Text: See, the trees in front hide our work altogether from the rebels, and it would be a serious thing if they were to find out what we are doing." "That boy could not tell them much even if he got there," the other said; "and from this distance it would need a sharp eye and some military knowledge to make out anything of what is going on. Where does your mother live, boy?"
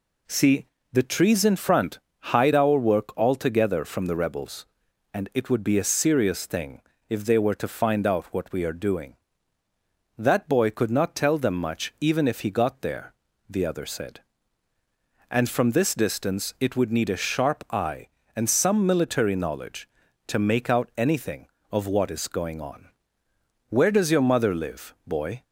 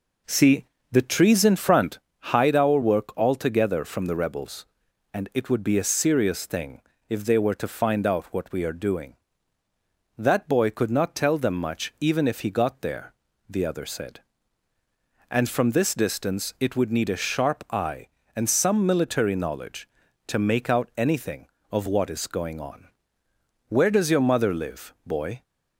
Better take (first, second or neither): first